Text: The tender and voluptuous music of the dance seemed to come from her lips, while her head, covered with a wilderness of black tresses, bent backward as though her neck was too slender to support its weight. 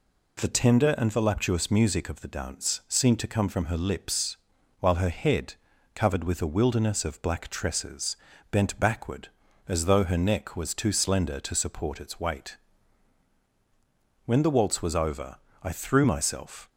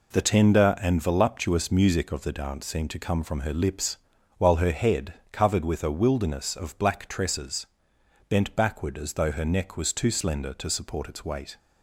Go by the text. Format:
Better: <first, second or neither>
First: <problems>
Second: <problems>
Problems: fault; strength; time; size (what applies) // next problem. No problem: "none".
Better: second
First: goes on to say "When the waltz was over I threw myself"; strong; from 14.2 s on; 2.4 s long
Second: none